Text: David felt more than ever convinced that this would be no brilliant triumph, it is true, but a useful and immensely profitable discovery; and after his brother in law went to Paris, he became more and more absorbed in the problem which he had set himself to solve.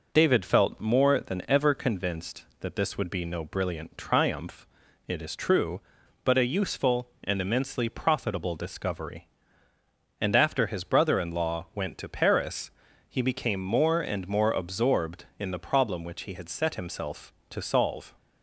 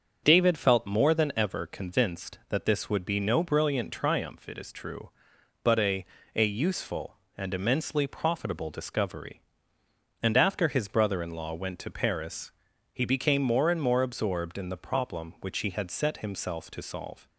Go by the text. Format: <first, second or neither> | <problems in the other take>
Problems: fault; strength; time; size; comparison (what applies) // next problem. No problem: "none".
first | starts louder than the rest; until 1.2 s; 7 dB // says "a" twice; at 6.3 s